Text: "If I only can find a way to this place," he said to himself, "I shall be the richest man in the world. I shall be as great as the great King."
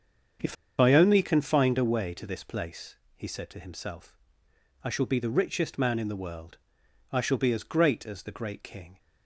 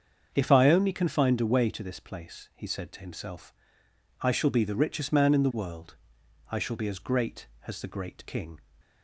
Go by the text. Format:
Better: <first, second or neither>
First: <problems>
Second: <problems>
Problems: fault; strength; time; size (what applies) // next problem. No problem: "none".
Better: second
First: starts louder than the rest; strong; until 1.6 s; 7 dB // pauses between "If" and "I"; slight; at 0.5 s; 0.24 s long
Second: starts louder than the rest; until 1.3 s; 7 dB